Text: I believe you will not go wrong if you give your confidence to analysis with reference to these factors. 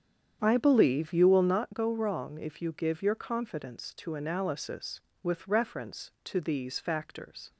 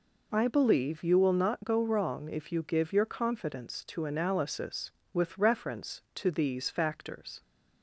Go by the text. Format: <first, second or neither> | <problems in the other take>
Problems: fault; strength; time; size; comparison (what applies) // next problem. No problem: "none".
second | starts louder than the rest; strong; until 1.7 s; 8.5 dB